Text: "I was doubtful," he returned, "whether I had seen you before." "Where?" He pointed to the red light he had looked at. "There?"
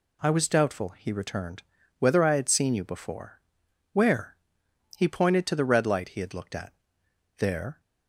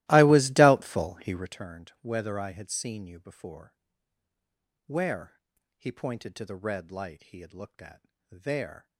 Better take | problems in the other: first | starts louder than the rest; strong; until 1.6 s; 17 dB

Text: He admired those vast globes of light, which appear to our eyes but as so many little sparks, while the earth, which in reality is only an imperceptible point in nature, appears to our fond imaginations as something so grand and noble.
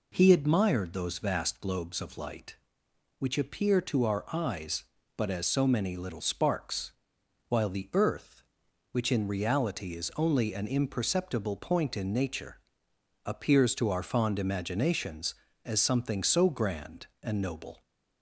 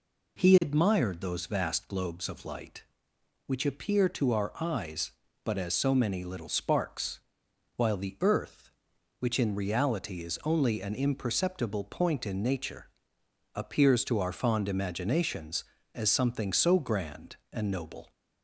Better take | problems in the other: neither | none

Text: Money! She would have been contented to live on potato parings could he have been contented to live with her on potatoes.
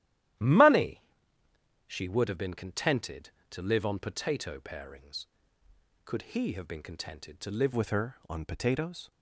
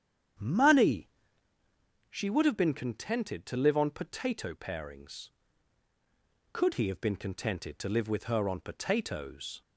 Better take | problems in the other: second | starts louder than the rest; strong; until 2.2 s; 13 dB; strong in the second // changes voice at "with"; from 7.7 s on; 1.4 s long

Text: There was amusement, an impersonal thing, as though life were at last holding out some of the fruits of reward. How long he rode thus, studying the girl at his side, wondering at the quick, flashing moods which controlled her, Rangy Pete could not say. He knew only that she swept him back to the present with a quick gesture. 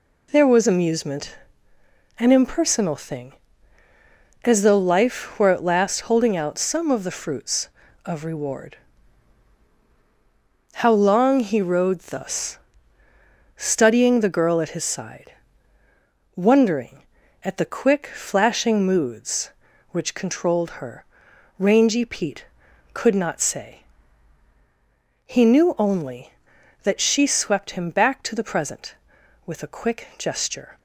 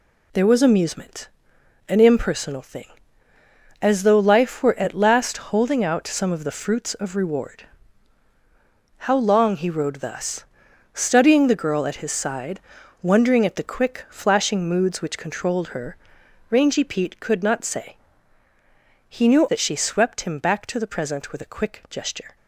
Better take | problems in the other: first | skips "only"; at 19.4 s

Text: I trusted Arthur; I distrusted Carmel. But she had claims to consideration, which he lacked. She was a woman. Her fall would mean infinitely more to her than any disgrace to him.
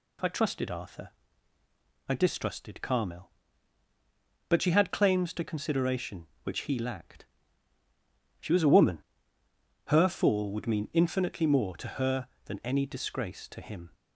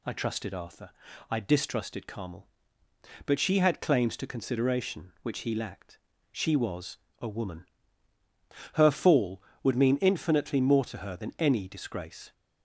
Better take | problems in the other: first | pauses between "was" and "a"; slight; at 6.9 s; 0.24 s long // stops before "to him"; at 12.3 s

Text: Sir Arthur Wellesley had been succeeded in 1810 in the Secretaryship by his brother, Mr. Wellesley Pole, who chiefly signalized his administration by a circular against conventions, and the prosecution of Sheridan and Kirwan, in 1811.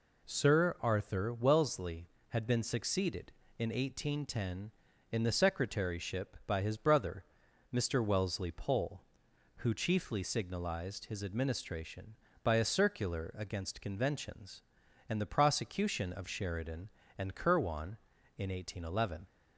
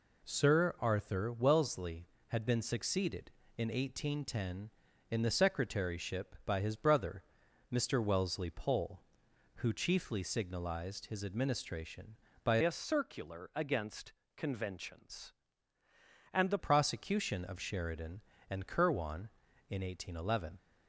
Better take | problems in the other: first | changes voice from "a" to "the"; from 12.6 to 16.5 s; 3.9 s long // pauses between "against" and "conventions"; slight; at 14.1 s; 0.24 s long

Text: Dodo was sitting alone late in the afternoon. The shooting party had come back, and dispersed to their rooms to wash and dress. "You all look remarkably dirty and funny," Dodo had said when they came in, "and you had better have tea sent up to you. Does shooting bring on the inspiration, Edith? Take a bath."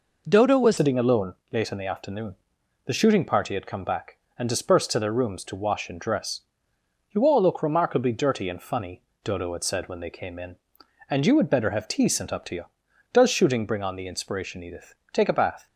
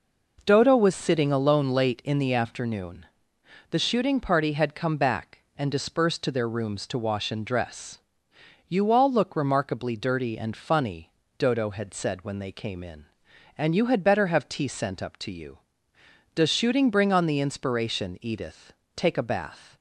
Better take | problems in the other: second | changes voice at "sitting"; from 0.7 s on; 14.9 s long // pauses between "alone" and "late"; slight; at 1.3 s; 0.16 s long

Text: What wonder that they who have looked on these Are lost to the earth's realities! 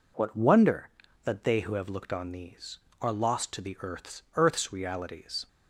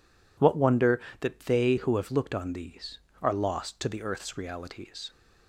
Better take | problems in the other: second | says "earth's" twice; at 4.3 s

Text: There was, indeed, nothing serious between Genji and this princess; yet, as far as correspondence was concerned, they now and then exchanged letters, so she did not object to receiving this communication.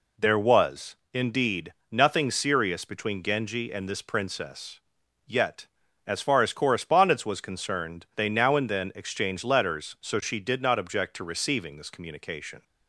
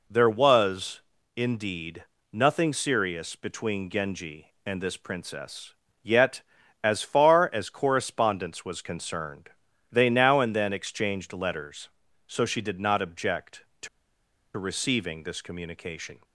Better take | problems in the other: first | pauses between "to" and "receiving"; noticeable; at 13.8 s; 0.68 s long

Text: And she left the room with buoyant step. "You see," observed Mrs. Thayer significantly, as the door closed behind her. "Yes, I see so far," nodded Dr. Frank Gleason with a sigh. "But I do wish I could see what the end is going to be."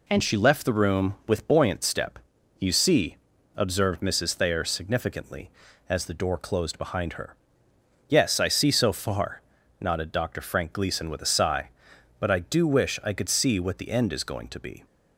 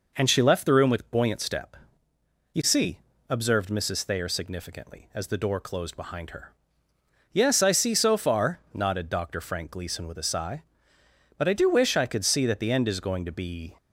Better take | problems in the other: first | says "that" for "what"; at 12.4 s

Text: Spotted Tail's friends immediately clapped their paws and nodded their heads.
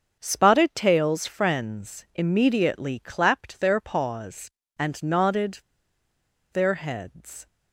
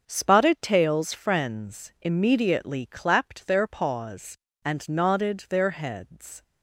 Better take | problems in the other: second | starts louder than the rest; strong; until 1.2 s; 7 dB; strong in the second // pauses between "nodded" and "their"; noticeable; at 5.6 s; 0.92 s long

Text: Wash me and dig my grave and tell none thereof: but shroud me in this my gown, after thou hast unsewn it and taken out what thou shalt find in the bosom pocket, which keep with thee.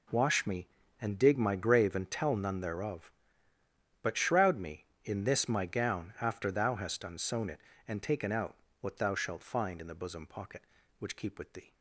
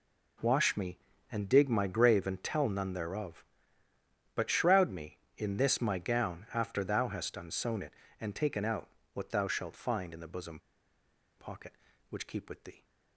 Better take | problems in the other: first | pauses between "out" and "what"; slight; at 8.8 s; 0.26 s long; slight in the first // pauses between "bosom" and "pocket"; noticeable; at 10.5 s; 0.78 s long

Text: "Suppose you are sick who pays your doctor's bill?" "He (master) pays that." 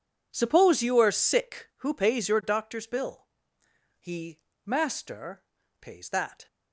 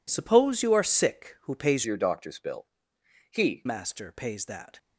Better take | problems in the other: first | changes voice from "your" to "He"; from 1.8 to 3.6 s; 1.8 s long

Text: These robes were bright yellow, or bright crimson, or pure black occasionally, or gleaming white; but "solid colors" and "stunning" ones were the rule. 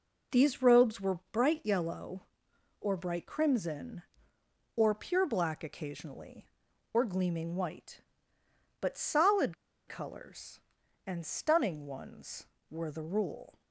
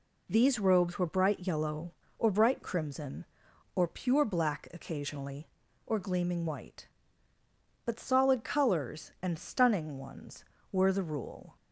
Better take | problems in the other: second | pauses between "solid" and "colors"; slight; at 9.5 s; 0.33 s long

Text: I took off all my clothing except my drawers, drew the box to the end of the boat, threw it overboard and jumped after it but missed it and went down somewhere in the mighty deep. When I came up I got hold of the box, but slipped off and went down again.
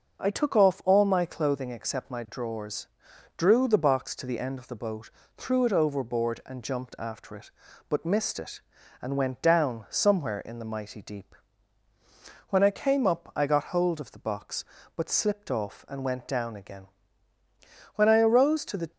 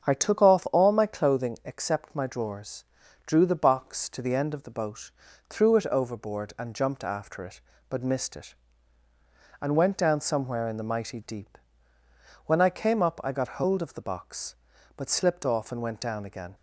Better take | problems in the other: second | starts louder than the rest; until 1.2 s; 6.5 dB; strong in the second // goes on to say "When I arose to the"; noticeable; from 17.9 s on; 0.96 s long

